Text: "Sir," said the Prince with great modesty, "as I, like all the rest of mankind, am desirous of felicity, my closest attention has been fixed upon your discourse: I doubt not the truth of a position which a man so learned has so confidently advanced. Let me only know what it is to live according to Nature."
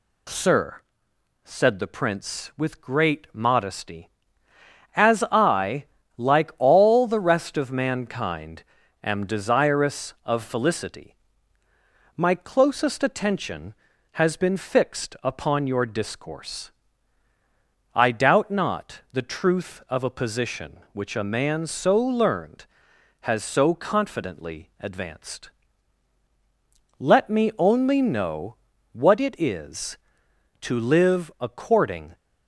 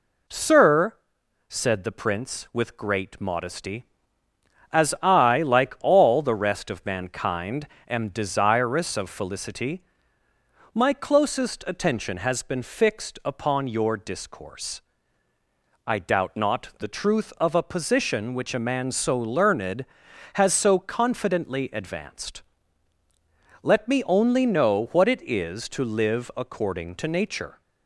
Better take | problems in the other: second | pauses between "know" and "what"; slight; at 28.5 s; 0.36 s long // stops before "to Nature"; at 32.1 s

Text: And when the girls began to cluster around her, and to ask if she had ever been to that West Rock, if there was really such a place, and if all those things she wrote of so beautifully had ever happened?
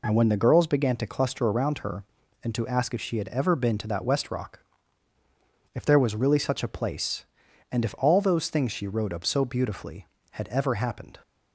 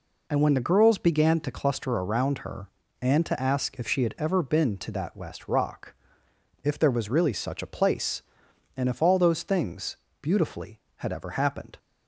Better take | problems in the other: first | skips "she wrote of so"; at 10.0 s

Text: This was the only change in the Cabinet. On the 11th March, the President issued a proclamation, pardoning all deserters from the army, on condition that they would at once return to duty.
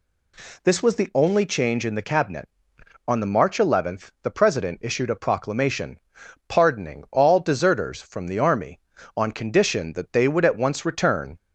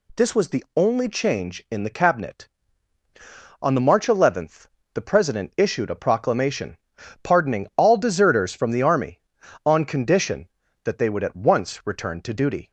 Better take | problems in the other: second | stops before "to duty"; at 11.3 s

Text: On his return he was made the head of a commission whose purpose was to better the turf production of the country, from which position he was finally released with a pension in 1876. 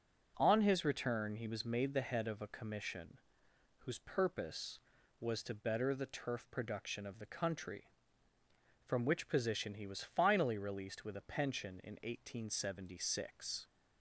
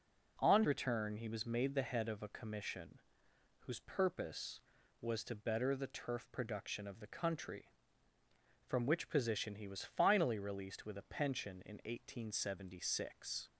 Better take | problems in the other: first | skips "his"; at 0.6 s // pauses between "commission" and "whose"; noticeable; at 3.0 s; 0.66 s long; noticeable in the first

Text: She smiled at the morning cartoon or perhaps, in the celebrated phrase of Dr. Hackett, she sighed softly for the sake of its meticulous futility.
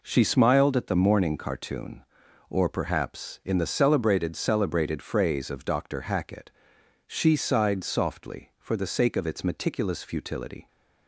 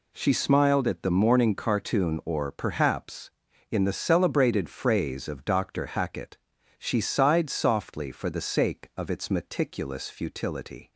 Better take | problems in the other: second | says "celebrated" twice; at 4.3 s

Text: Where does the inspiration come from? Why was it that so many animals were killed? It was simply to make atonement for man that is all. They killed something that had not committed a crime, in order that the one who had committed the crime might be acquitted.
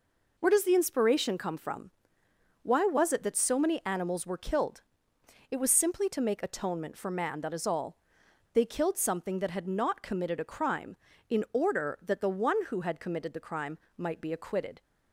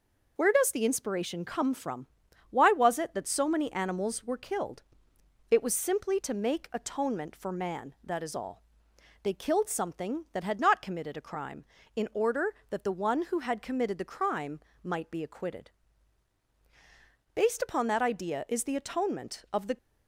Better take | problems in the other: first | pauses between "crime" and "might"; slight; at 14.5 s; 0.24 s long; slight in the first // goes on to say "Based upon that idea is the atonement of the"; strong; from 17.3 s on; 2.4 s long

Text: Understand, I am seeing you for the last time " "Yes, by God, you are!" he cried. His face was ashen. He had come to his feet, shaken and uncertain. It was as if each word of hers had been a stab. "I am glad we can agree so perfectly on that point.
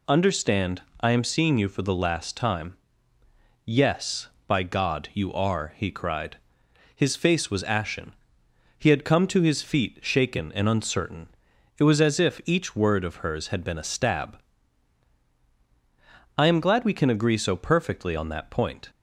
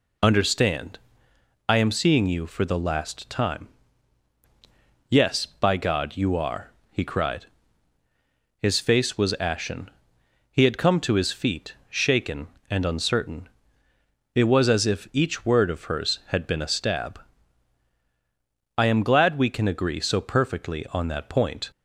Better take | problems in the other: neither | none

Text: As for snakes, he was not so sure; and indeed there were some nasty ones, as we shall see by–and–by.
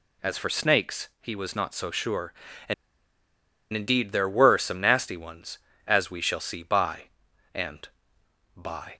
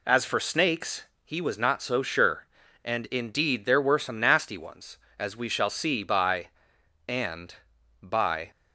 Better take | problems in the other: second | pauses between "and" and "indeed"; at 2.7 s; 0.99 s long

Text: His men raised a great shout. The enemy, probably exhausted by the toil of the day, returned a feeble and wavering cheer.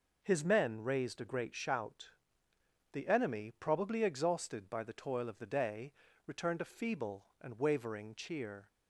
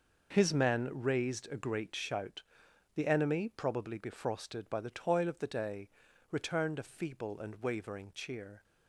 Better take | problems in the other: first | says "befrosted" for "exhausted"; at 3.9 s

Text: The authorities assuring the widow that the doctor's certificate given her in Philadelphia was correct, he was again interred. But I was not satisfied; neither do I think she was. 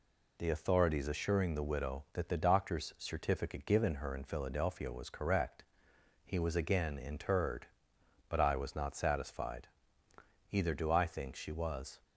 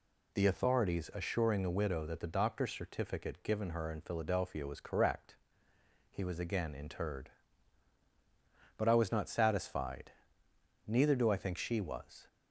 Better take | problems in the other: second | says "either" for "neither"; at 10.4 s

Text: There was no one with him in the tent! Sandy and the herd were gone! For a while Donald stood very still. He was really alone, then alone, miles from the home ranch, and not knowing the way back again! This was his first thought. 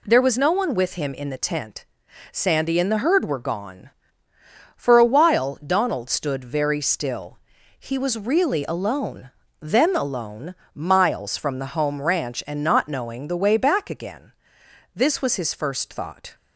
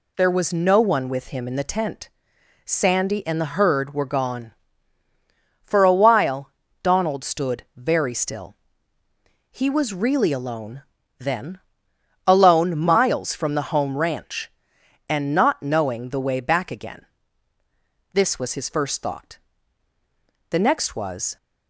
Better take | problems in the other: first | pauses between "while" and "Donald"; slight; at 6.5 s; 0.32 s long // pauses between "then" and "alone"; noticeable; at 11.5 s; 0.68 s long // goes on to say "The next was"; noticeable; from 20.5 s on; 0.86 s long

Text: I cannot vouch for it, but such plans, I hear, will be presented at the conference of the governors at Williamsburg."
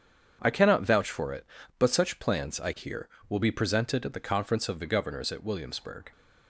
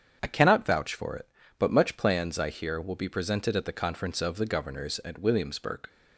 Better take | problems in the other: first | starts louder than the rest; strong; until 1.2 s; 7.5 dB; strong in the first // says "much" for "such"; at 1.6 s

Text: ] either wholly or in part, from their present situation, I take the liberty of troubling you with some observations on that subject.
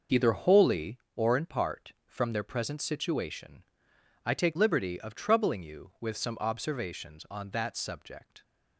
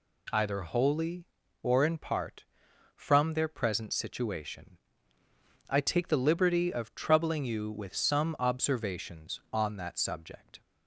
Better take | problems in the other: second | skips "the"; at 4.5 s

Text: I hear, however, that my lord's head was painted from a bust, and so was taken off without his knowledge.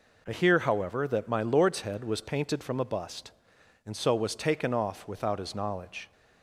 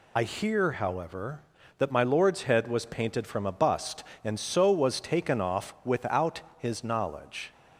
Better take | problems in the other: first | loses the start of "I"; at 0.1 s; 45 ms // pauses between "without" and "his"; slight; at 6.4 s; 0.16 s long

